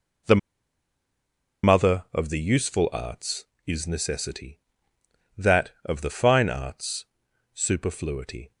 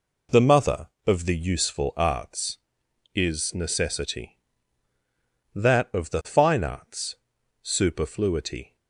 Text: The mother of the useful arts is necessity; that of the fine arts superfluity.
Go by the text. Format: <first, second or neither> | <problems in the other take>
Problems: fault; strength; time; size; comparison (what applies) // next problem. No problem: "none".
second | pauses between "The" and "mother"; strong; at 0.3 s; 1.2 s long // pauses between "arts" and "superfluity"; noticeable; at 7.0 s; 0.48 s long; also in the second